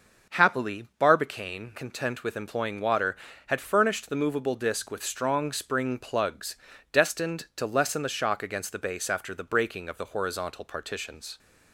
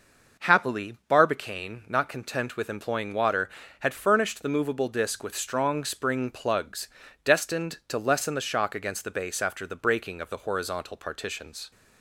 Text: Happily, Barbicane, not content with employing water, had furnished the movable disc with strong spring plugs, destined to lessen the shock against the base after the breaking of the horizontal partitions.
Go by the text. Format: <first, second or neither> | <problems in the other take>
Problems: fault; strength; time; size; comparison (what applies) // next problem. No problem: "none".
second | skips "not"; at 1.7 s